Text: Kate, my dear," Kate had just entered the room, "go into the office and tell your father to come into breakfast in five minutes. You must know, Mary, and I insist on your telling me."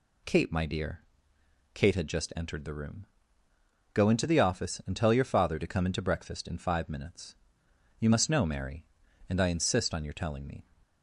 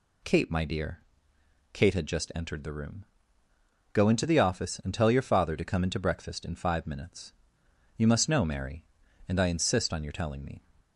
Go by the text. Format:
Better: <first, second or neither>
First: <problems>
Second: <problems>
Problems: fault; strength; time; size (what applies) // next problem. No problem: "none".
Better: neither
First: none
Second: none